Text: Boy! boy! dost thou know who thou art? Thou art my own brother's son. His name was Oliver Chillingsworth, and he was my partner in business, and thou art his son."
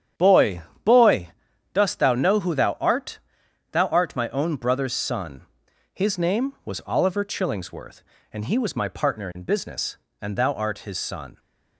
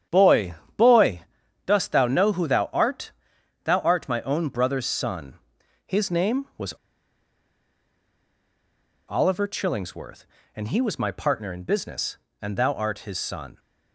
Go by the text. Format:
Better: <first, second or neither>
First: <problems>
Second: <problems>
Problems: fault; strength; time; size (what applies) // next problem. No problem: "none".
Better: first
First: starts louder than the rest; strong; until 1.8 s; 9 dB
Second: starts louder than the rest; strong; until 1.8 s; 9 dB // pauses between "was" and "Oliver"; strong; at 6.7 s; 2.3 s long